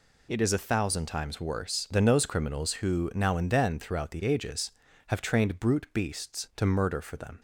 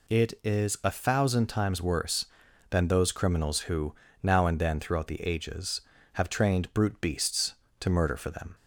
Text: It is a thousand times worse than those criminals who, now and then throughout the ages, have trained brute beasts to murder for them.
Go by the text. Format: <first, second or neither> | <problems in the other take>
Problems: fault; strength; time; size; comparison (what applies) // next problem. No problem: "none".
neither | none